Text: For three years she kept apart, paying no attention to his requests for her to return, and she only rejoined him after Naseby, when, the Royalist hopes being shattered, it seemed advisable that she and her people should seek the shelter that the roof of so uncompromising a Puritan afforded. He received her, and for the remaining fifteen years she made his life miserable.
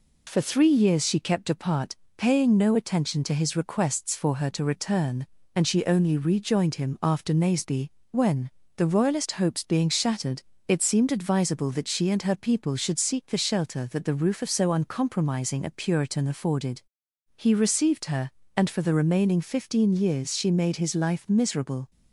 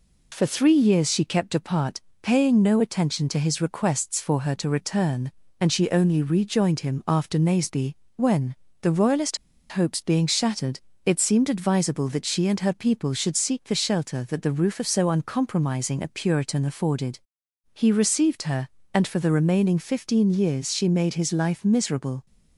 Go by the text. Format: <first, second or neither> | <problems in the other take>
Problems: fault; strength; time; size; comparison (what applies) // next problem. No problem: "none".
first | pauses between "Royalist" and "hopes"; slight; at 9.3 s; 0.32 s long